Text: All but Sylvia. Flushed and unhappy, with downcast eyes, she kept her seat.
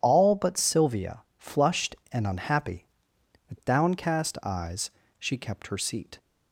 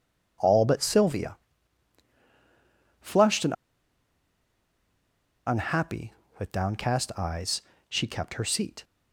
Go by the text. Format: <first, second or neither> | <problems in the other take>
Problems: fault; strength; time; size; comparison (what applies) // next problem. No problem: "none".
first | pauses between "and" and "unhappy"; strong; at 3.5 s; 1.9 s long